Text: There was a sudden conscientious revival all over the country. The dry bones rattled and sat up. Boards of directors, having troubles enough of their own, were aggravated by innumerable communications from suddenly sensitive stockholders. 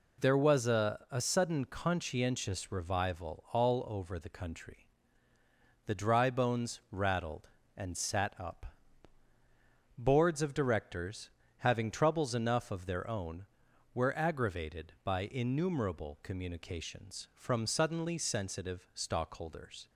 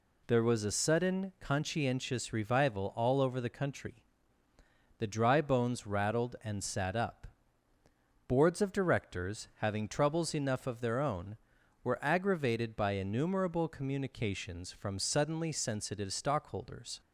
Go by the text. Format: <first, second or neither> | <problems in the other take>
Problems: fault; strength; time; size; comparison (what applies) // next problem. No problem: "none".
second | says "a" twice; at 1.0 s